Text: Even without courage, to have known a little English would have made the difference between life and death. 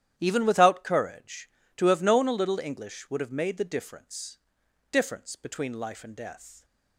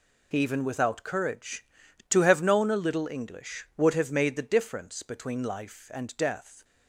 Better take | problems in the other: second | starts louder than the rest; strong; until 1.1 s; 11.5 dB // says "difference" twice; at 4.9 s

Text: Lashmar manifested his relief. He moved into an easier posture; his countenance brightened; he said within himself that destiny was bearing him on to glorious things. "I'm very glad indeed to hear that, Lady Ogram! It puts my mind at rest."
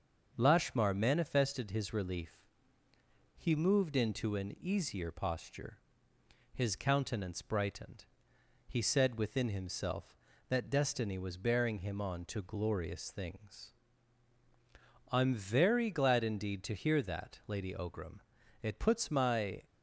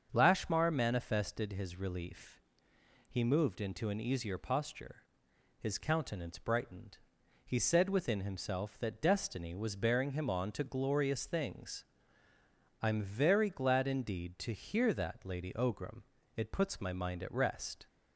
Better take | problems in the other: second | starts louder than the rest; until 1.3 s; 6.5 dB; also in the second // stops before "mind at rest"; at 19.6 s

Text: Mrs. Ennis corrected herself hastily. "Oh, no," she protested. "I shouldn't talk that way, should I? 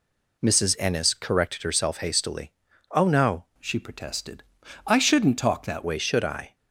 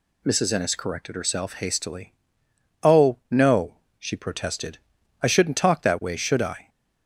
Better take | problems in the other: second | changes voice from "she" to "that"; from 3.5 to 5.8 s; 2.3 s long

